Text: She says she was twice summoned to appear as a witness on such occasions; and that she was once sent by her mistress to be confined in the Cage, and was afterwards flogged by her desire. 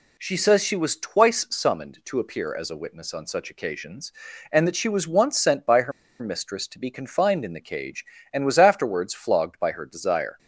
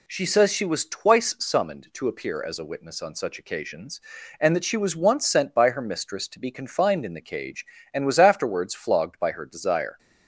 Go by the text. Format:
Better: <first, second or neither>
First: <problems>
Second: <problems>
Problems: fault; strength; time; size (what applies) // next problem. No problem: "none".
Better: second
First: pauses between "her" and "mistress"; slight; at 5.9 s; 0.28 s long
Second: none